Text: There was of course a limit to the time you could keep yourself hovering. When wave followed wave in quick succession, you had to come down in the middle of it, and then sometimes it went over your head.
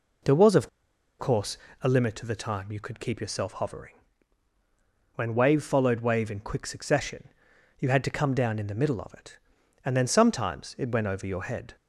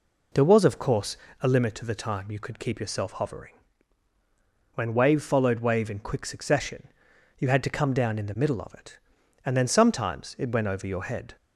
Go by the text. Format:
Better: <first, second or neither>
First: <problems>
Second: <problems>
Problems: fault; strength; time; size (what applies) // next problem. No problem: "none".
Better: second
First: pauses between "of" and "course"; noticeable; at 0.6 s; 0.50 s long // pauses between "course" and "a"; slight; at 1.5 s; 0.26 s long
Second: pauses between "course" and "a"; slight; at 1.1 s; 0.26 s long